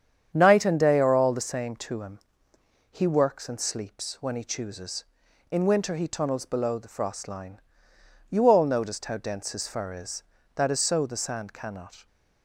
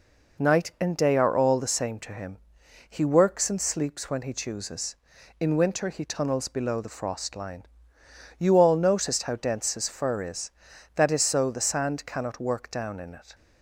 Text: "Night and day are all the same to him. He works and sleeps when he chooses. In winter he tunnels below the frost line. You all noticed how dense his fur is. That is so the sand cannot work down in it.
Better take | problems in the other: second | starts louder than the rest; strong; until 1.3 s; 8.5 dB // stops before "work down in it"; at 12.0 s

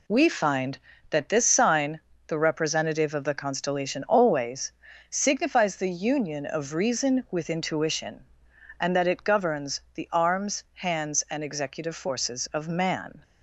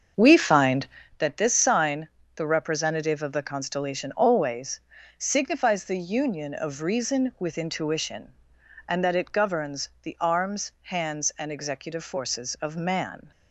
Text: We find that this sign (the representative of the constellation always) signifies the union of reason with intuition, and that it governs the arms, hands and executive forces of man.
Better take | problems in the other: first | starts louder than the rest; until 1.1 s; 7 dB

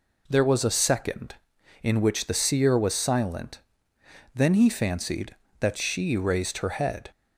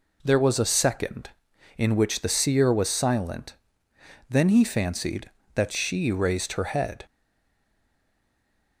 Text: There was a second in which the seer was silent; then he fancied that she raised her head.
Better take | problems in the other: first | stays silent after the last word; noticeable; from 7.0 s on; 1.8 s long

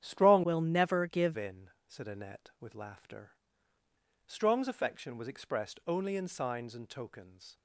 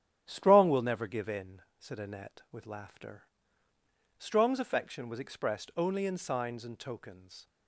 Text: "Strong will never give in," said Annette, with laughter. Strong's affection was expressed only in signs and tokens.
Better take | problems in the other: second | starts louder than the rest; strong; until 1.0 s; 9.5 dB; strong in the second // changes voice from "will" to "give"; from 0.4 to 1.3 s; 0.9 s long

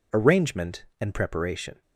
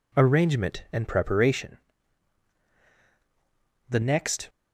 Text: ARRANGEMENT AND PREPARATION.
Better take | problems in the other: first | goes on to say "The next"; from 3.8 s on; 0.61 s long

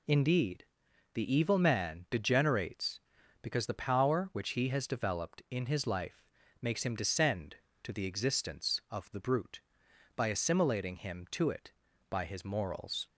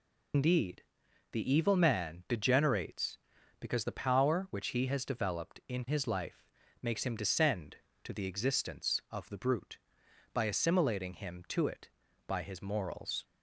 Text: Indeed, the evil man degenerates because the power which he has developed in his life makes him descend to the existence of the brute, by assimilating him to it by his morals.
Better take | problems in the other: first | loses the start of "Indeed"; at 0.3 s; 95 ms // pauses between "life" and "makes"; slight; at 6.4 s; 0.34 s long; slight in the first

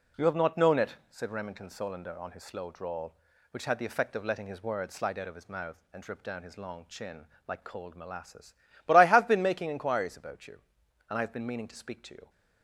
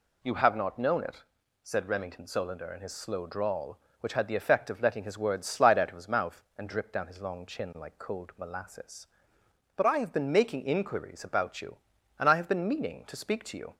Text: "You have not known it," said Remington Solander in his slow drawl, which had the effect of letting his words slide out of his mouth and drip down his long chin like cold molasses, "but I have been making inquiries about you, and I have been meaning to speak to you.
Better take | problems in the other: second | says "on" for "in"; at 2.1 s // pauses between "chin" and "like"; slight; at 7.2 s; 0.20 s long

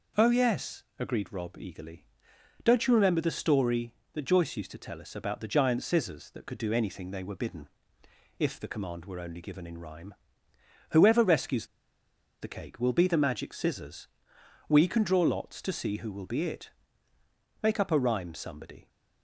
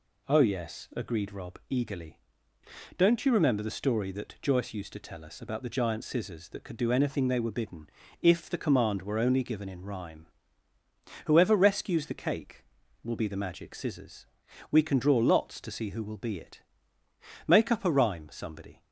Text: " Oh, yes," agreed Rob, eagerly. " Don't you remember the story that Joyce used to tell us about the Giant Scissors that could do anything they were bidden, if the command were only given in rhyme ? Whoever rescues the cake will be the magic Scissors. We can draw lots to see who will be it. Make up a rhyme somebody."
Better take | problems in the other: second | pauses between "rescues" and "the"; noticeable; at 11.6 s; 0.74 s long

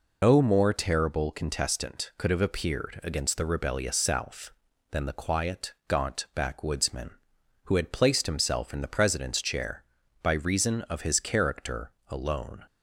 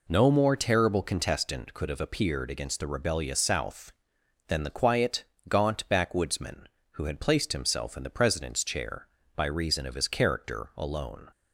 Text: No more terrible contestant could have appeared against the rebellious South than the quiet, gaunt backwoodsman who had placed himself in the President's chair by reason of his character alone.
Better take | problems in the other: second | loses the start of "No"; at 0.2 s; 115 ms // pauses between "character" and "alone"; slight; at 11.9 s; 0.16 s long

